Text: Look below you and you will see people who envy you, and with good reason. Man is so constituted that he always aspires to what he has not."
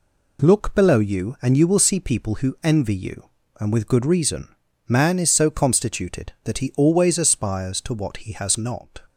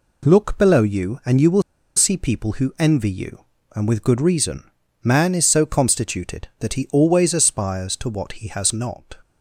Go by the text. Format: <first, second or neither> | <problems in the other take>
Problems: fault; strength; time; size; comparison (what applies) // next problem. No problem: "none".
first | pauses between "will" and "see"; slight; at 1.6 s; 0.34 s long